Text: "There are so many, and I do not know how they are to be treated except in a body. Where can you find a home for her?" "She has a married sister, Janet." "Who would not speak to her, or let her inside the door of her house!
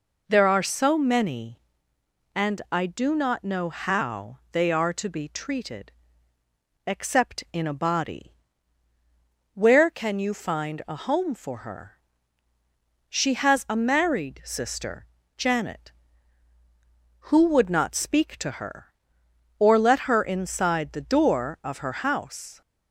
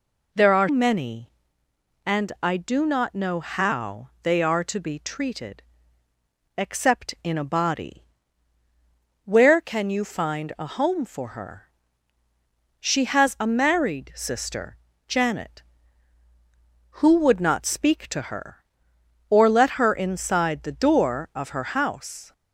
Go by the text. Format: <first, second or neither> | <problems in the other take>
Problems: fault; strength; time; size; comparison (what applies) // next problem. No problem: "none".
first | skips "so"; at 0.6 s // pauses between "treated" and "except"; noticeable; at 5.6 s; 0.96 s long; noticeable in the first